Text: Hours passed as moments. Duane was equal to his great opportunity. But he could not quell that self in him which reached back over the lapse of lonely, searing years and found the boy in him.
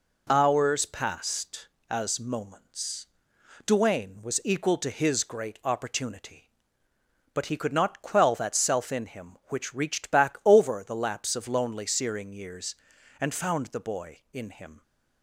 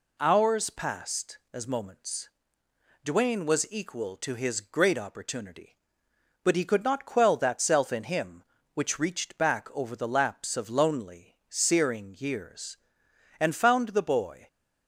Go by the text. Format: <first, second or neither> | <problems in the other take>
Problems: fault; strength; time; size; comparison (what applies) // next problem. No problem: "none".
first | stops before "in him"; at 14.4 s